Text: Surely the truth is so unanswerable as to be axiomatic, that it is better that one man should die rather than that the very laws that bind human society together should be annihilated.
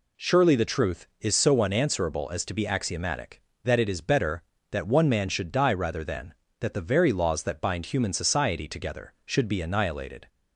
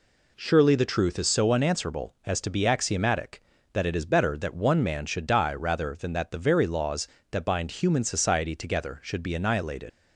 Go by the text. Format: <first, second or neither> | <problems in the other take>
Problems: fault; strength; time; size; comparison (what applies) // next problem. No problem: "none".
first | leaves "annihilated" unfinished; at 9.8 s; 100 ms